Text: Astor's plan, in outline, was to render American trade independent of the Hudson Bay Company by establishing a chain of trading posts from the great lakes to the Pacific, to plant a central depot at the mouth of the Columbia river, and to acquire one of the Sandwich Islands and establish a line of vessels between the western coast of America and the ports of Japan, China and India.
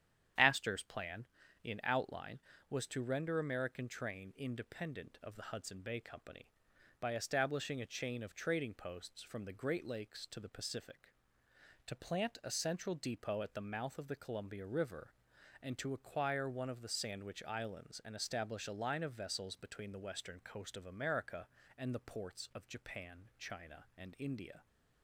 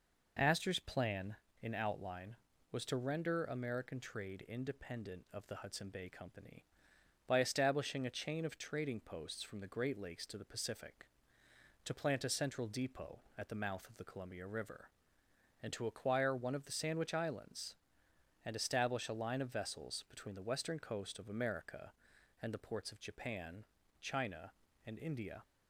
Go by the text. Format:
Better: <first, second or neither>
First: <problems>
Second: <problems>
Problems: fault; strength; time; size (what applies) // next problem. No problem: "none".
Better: second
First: starts louder than the rest; strong; until 1.7 s; 9.5 dB // says "train" for "trade"; at 3.8 s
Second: none